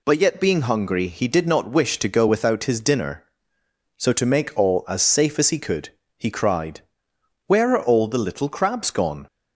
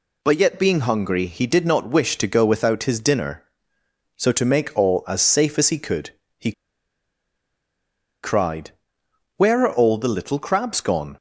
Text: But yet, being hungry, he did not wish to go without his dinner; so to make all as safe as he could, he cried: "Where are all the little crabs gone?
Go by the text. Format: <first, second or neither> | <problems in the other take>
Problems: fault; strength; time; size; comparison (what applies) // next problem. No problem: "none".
first | pauses between "he" and "cried"; strong; at 6.5 s; 1.7 s long